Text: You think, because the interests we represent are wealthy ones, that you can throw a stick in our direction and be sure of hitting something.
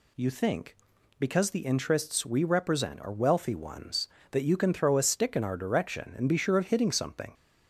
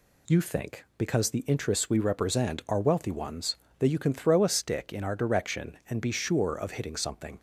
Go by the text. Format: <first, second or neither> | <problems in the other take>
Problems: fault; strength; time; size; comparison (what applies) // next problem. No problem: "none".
neither | none